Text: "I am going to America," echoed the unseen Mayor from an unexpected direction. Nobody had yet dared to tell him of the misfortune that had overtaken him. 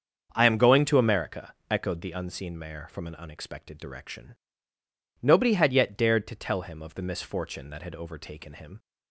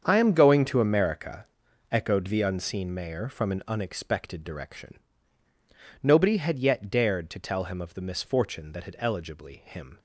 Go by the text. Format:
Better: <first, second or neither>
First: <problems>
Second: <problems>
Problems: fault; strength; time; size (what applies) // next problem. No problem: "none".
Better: first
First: starts louder than the rest; until 1.3 s; 7 dB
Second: starts louder than the rest; strong; until 1.0 s; 7.5 dB // says "eligibly" for "overtaken"; at 8.9 s